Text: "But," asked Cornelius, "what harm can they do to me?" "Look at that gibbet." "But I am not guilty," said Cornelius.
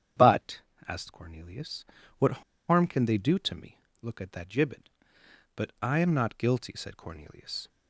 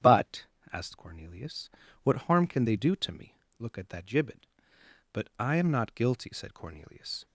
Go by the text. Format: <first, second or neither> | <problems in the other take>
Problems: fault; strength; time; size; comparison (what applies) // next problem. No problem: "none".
second | starts louder than the rest; strong; until 1.4 s; 9 dB; strong in the second // pauses between "what" and "harm"; slight; at 2.4 s; 0.26 s long